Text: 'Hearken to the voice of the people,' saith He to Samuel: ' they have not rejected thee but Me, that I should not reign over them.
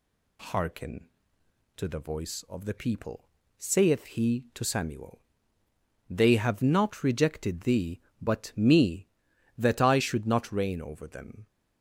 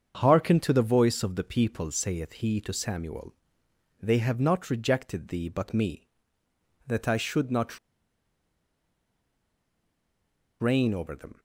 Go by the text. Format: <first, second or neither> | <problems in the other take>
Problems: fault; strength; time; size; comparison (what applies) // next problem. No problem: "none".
first | starts louder than the rest; strong; until 1.1 s; 7.5 dB // pauses between "not" and "reign"; strong; at 7.7 s; 2.8 s long